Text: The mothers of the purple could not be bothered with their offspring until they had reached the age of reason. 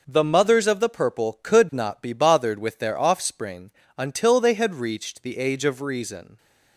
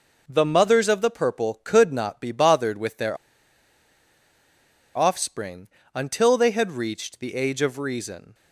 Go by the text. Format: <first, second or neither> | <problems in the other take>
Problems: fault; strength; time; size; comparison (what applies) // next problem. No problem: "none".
first | pauses between "their" and "offspring"; strong; at 3.1 s; 1.7 s long // pauses between "offspring" and "until"; slight; at 5.6 s; 0.26 s long; slight in the first